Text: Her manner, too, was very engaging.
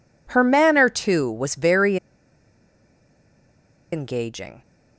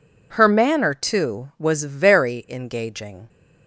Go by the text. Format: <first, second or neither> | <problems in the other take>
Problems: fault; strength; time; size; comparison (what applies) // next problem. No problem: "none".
second | pauses between "very" and "engaging"; strong; at 1.9 s; 1.9 s long